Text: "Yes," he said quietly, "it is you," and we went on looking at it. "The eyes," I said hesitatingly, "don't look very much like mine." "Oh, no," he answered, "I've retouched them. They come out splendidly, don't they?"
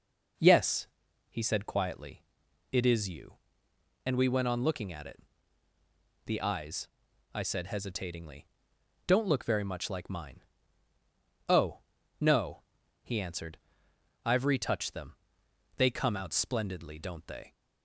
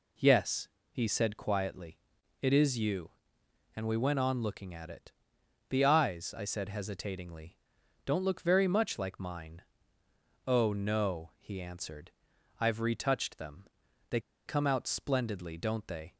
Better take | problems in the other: first | pauses between "They" and "come"; slight; at 14.1 s; 0.27 s long

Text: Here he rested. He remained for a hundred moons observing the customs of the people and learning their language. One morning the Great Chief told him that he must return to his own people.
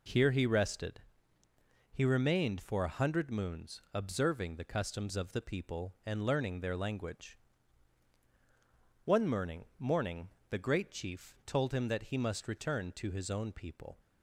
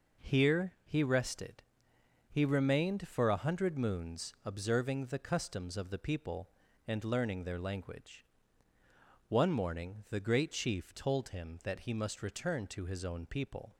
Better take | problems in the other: second | says "morning" twice; at 9.7 s

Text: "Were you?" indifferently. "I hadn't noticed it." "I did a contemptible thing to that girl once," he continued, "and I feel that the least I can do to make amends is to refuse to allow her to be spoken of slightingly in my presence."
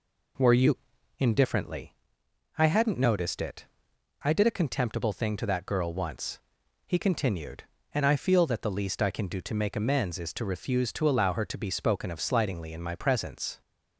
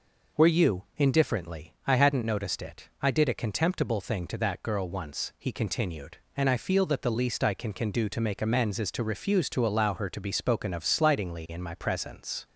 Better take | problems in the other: first | says "can" twice; at 7.7 s

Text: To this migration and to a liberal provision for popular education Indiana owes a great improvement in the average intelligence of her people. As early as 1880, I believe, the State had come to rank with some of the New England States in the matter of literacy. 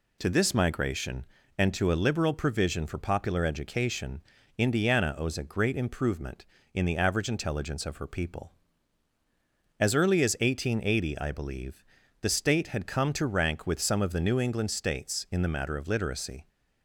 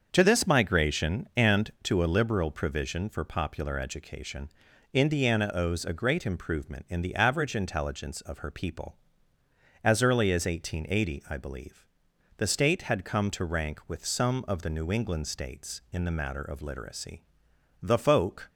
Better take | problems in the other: first | starts louder than the rest; until 1.1 s; 7 dB // pauses between "education" and "Indiana"; at 4.4 s; 0.42 s long; slight in the first // goes on to say "The folk"; noticeable; from 17.8 s on; 0.66 s long

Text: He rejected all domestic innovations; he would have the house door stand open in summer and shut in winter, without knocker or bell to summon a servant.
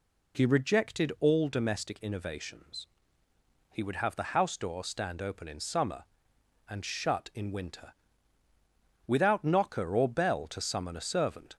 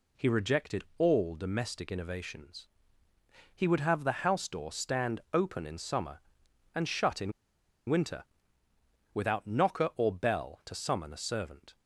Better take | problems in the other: first | pauses between "in" and "winter"; noticeable; at 7.3 s; 0.57 s long

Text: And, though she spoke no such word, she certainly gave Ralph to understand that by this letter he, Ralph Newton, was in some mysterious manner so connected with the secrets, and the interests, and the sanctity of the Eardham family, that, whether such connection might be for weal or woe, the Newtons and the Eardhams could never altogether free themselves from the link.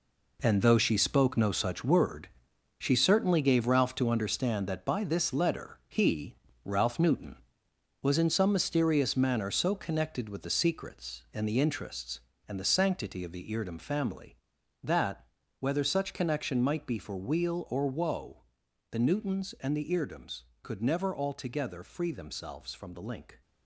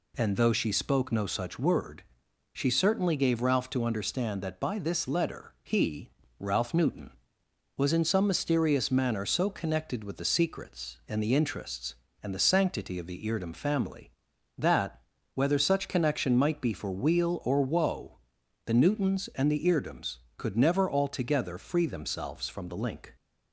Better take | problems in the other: second | gets quieter; strong; throughout; 10 dB

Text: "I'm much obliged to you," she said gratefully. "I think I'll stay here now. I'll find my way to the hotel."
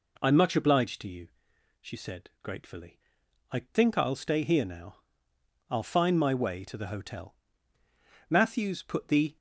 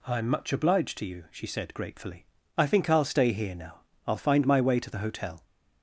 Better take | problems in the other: second | goes on to say "Matthews put the"; noticeable; from 8.3 s on; 1.0 s long

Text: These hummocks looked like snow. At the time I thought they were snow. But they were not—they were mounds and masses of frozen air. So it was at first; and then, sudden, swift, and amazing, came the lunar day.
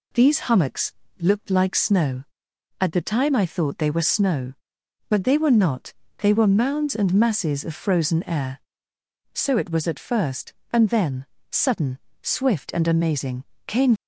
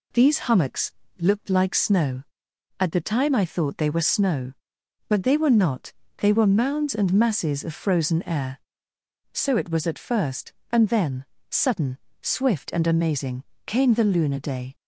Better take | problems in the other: second | pauses between "hummocks" and "looked"; slight; at 0.9 s; 0.30 s long; slight in the second // stops before "the lunar day"; at 13.9 s

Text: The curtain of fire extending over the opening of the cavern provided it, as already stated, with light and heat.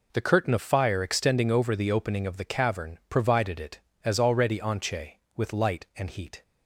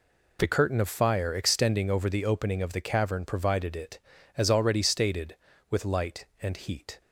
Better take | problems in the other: second | says "anche" for "stated"; at 4.5 s

